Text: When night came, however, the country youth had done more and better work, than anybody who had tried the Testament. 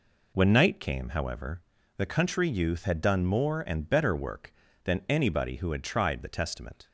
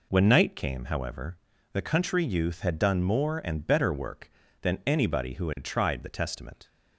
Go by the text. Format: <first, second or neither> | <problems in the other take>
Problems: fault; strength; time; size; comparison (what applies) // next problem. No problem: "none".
neither | none